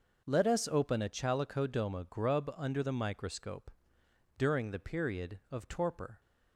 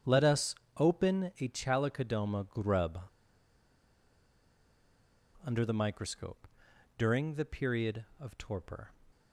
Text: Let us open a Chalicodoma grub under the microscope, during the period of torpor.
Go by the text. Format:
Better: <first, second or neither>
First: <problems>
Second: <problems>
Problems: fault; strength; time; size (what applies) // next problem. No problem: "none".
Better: first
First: none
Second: starts louder than the rest; strong; until 1.2 s; 8.5 dB // pauses between "us" and "open"; slight; at 0.5 s; 0.22 s long // pauses between "grub" and "under"; strong; at 2.9 s; 2.4 s long